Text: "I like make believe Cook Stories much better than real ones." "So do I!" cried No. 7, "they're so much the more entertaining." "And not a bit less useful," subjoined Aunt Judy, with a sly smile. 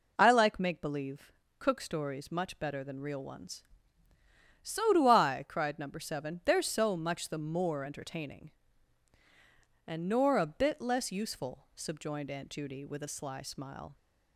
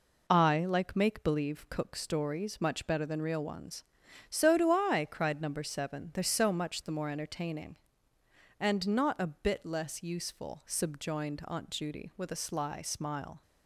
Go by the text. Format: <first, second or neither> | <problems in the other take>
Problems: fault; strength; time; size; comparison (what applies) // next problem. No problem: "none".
second | pauses between "believe" and "Cook"; slight; at 1.2 s; 0.28 s long // says "nor" for "not"; at 10.0 s